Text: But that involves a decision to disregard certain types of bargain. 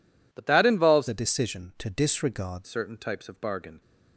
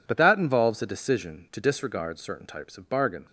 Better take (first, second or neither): second